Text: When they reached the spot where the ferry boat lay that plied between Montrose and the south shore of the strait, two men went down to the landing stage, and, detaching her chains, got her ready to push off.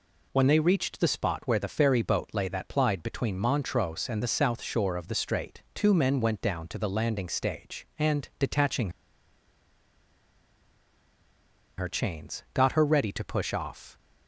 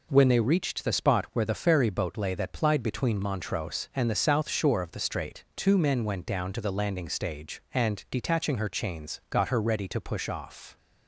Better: second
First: pauses between "detaching" and "her"; strong; at 8.8 s; 2.8 s long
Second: none

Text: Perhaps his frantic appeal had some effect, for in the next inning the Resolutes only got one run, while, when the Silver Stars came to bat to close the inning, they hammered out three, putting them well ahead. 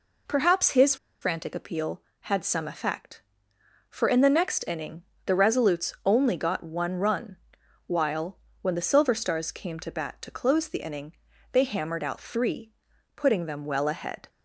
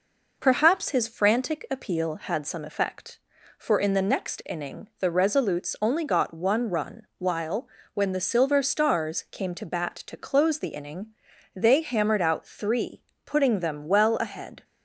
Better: second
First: pauses between "his" and "frantic"; slight; at 0.9 s; 0.26 s long // pauses between "inning" and "the"; slight; at 5.0 s; 0.24 s long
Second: none

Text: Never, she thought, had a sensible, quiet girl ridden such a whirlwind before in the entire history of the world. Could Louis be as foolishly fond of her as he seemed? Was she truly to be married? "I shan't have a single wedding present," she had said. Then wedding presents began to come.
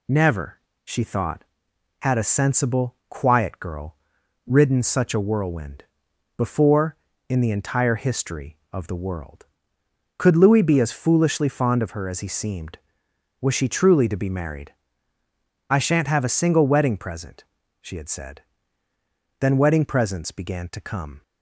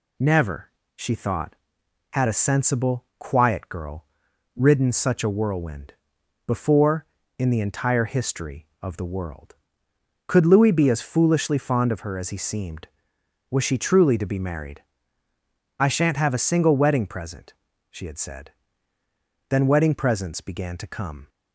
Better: neither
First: pauses between "girl" and "ridden"; noticeable; at 3.9 s; 0.52 s long // pauses between "whirlwind" and "before"; noticeable; at 5.8 s; 0.54 s long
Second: pauses between "girl" and "ridden"; noticeable; at 4.0 s; 0.52 s long // pauses between "whirlwind" and "before"; noticeable; at 5.9 s; 0.54 s long

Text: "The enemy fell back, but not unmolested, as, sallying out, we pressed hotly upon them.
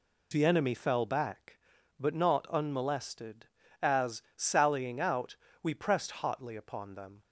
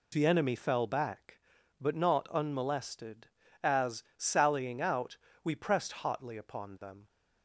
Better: neither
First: none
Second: none

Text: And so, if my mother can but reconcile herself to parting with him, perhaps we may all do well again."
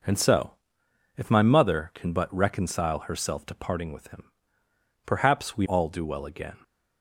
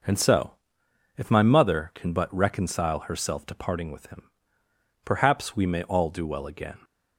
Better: second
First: skips "may"; at 5.6 s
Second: none

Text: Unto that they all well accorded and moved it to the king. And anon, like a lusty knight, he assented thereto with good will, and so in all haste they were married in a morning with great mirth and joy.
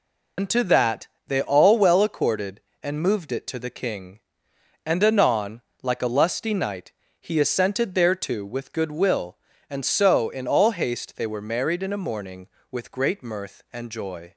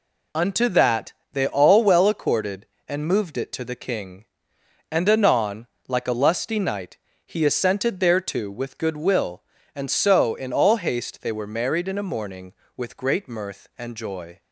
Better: second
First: loses the start of "Unto"; at 0.3 s; 95 ms // pauses between "that" and "they"; slight; at 1.0 s; 0.20 s long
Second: pauses between "that" and "they"; slight; at 1.1 s; 0.20 s long

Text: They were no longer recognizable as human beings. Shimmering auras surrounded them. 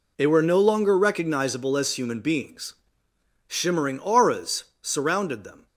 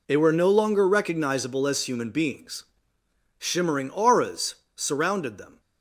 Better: neither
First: pauses between "auras" and "surrounded"; slight; at 4.6 s; 0.18 s long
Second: pauses between "auras" and "surrounded"; slight; at 4.5 s; 0.20 s long

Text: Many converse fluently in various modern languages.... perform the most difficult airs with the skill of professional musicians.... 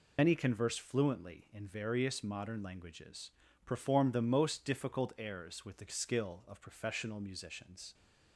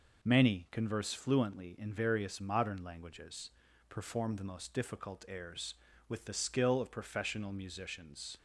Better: second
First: loses the start of "Many"; at 0.1 s; 50 ms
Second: none

